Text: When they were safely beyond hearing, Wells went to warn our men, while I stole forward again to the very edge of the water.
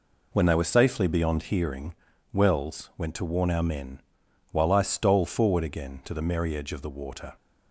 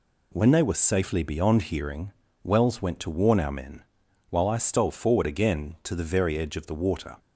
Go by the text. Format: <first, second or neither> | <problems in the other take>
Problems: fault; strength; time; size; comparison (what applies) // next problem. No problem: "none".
second | says "merry" for "very"; at 6.2 s